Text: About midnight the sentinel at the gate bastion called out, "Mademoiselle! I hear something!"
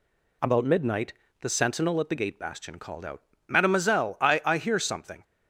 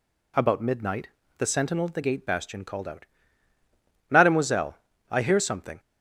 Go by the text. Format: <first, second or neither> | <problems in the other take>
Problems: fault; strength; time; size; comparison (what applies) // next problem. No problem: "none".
second | pauses between "midnight" and "the"; slight; at 1.1 s; 0.30 s long; slight in the second // says "I" twice; at 4.4 s